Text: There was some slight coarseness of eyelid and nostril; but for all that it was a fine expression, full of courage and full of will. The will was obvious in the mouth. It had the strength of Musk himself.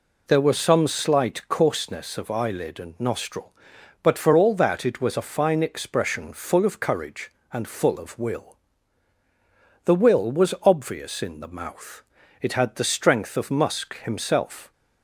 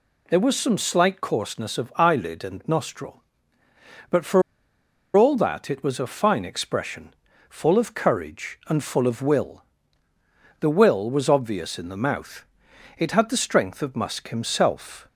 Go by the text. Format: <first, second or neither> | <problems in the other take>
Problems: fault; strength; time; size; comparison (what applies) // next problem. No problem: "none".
first | pauses between "for" and "all"; noticeable; at 4.4 s; 0.73 s long